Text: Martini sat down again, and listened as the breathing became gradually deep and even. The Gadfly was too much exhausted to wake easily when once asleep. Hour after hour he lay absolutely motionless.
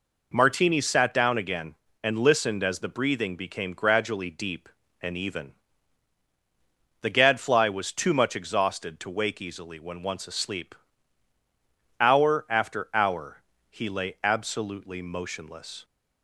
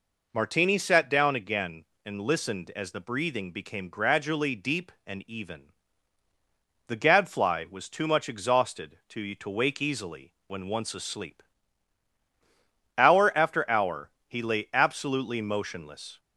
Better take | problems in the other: first | says "to" twice; at 9.3 s // pauses between "hour" and "he"; slight; at 14.1 s; 0.16 s long; slight in the first

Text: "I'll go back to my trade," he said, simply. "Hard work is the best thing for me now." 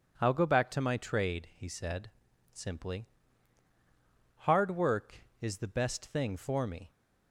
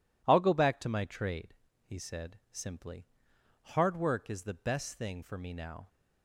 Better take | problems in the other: second | stops before "now"; at 6.8 s

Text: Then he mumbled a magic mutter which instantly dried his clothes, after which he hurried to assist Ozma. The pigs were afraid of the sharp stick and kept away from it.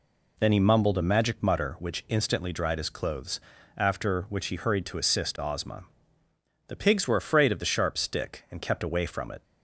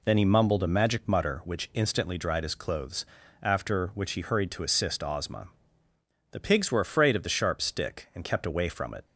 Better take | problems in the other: neither | none

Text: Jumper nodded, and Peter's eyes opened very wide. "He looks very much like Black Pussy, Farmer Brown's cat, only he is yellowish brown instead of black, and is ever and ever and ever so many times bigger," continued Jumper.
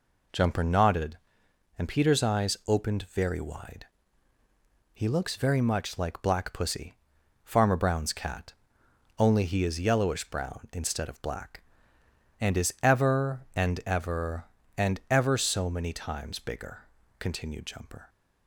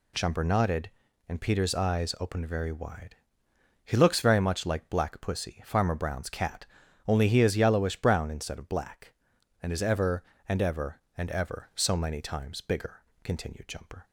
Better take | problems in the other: neither | none

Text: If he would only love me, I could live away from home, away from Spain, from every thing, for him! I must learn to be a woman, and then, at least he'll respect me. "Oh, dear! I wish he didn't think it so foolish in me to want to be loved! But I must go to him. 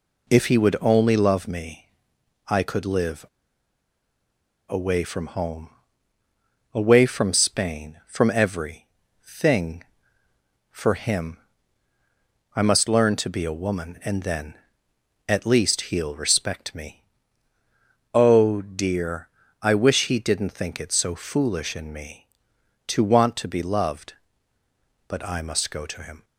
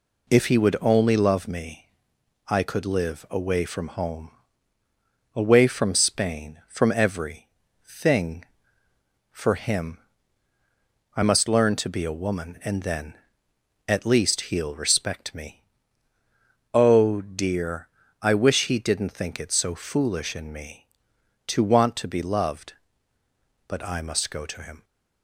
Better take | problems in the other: second | pauses between "live" and "away"; strong; at 3.2 s; 1.4 s long // pauses between "every" and "thing"; at 8.8 s; 0.38 s long; also in the second

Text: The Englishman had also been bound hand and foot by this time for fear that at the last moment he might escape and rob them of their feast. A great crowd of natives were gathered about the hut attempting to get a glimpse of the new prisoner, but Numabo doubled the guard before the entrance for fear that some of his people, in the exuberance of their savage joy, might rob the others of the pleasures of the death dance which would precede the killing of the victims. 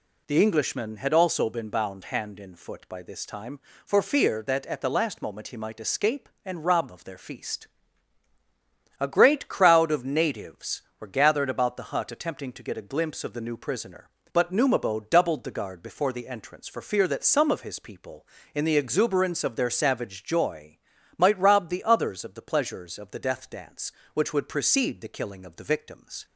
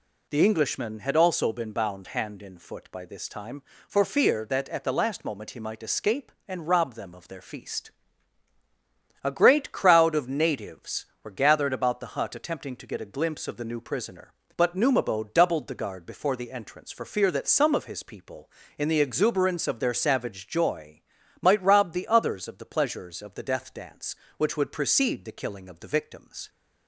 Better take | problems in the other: second | skips "them"; at 6.8 s

